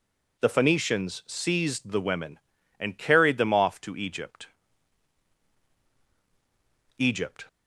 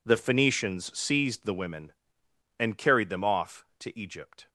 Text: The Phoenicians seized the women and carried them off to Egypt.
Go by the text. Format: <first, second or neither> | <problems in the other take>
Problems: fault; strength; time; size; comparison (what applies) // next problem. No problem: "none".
second | says "Egypt" twice; at 6.9 s